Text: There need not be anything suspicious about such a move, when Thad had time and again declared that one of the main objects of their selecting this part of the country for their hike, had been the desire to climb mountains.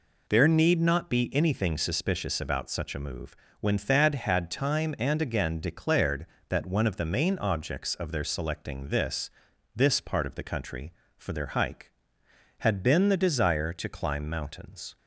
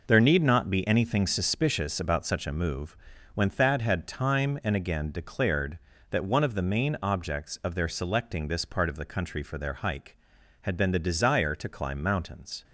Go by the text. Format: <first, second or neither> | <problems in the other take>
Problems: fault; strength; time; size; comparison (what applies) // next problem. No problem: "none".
second | says "this" twice; at 9.7 s